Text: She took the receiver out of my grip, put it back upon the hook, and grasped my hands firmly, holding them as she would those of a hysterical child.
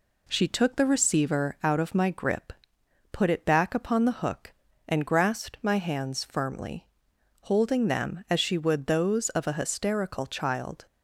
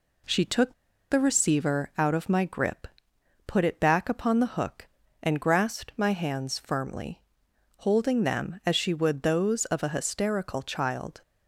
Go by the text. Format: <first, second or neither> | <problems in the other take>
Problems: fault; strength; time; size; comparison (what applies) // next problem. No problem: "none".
first | pauses between "took" and "the"; at 0.7 s; 0.37 s long